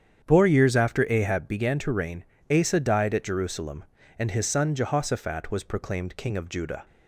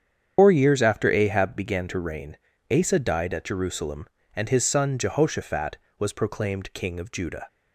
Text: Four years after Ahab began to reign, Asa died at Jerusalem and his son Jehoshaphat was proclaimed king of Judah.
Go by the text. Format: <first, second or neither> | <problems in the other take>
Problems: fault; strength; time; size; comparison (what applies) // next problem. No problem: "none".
first | loses the start of "Four"; at 0.3 s; 115 ms // starts louder than the rest; strong; until 1.3 s; 8 dB; strong in the first